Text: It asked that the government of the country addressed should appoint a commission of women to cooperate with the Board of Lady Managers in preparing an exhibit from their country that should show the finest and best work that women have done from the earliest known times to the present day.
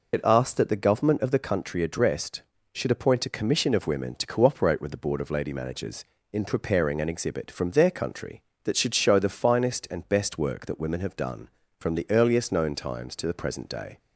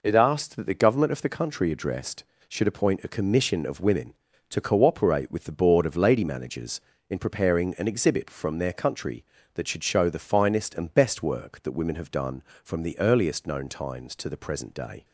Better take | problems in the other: second | loses the start of "It"; at 0.1 s; 45 ms

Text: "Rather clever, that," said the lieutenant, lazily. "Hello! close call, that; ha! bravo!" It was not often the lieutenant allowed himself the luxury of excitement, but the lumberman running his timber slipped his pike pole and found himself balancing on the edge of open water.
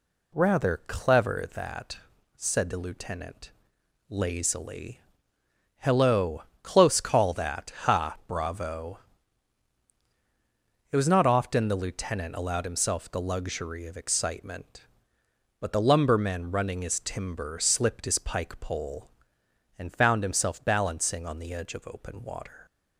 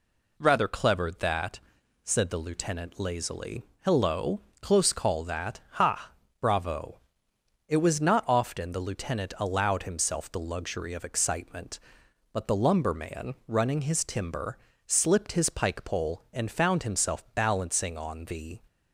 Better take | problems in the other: first | pauses between "timber" and "slipped"; slight; at 14.5 s; 0.26 s long // stops before "edge of open water"; at 18.6 s

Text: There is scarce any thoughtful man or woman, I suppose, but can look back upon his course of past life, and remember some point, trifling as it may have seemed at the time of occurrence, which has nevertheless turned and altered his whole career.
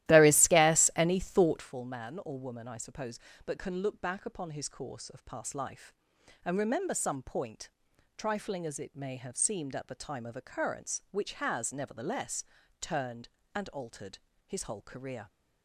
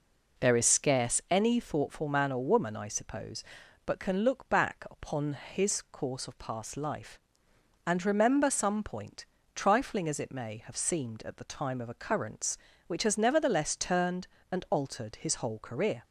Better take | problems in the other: second | starts louder than the rest; strong; until 1.7 s; 14.5 dB // pauses between "nevertheless" and "turned"; slight; at 12.4 s; 0.36 s long // pauses between "altered" and "his"; slight; at 14.1 s; 0.28 s long

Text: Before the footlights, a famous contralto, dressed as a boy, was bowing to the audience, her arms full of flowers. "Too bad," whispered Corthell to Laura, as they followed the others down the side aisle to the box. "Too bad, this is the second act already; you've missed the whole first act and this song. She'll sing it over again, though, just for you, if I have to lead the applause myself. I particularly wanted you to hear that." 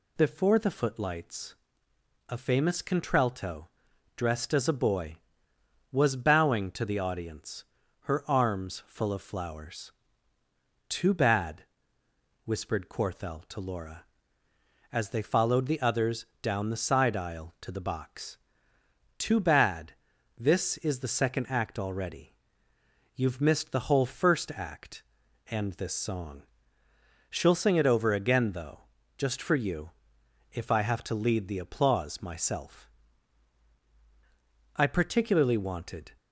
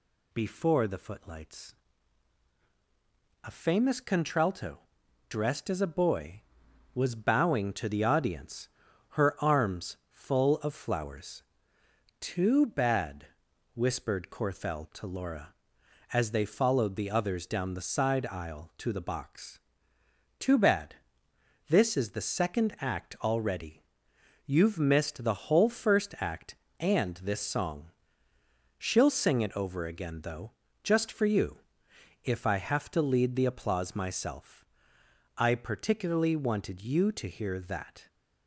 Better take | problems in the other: second | pauses between "others" and "down"; slight; at 16.2 s; 0.16 s long // stops before "you to hear that"; at 36.1 s

